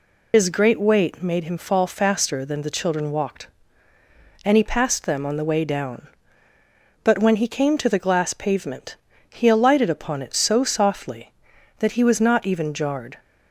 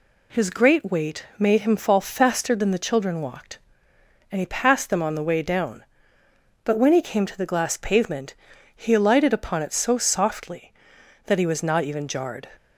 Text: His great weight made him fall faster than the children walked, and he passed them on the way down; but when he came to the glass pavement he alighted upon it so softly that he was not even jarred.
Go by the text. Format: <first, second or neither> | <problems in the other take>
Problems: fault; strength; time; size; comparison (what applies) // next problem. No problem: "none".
second | loses the start of "His"; at 0.3 s; 90 ms // pauses between "pavement" and "he"; slight; at 8.9 s; 0.34 s long; also in the second